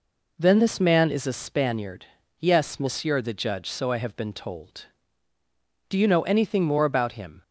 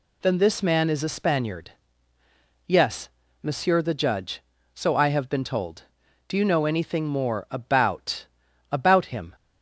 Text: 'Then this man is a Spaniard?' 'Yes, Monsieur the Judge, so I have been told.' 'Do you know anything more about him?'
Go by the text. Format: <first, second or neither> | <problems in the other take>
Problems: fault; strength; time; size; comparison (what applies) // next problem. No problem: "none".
first | says "about" twice; at 8.6 s